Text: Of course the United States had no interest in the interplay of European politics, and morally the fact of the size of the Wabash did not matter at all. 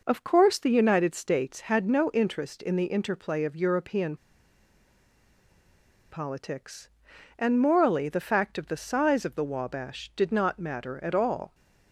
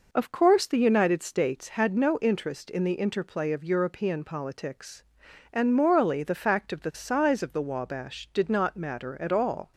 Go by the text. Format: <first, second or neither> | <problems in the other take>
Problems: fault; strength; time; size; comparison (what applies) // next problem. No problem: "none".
second | pauses between "European" and "politics"; strong; at 4.1 s; 1.9 s long